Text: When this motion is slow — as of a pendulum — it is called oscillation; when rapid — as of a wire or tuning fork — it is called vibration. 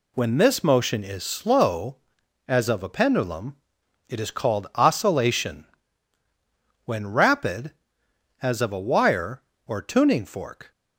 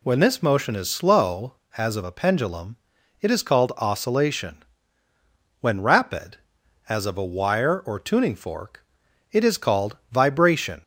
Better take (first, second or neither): second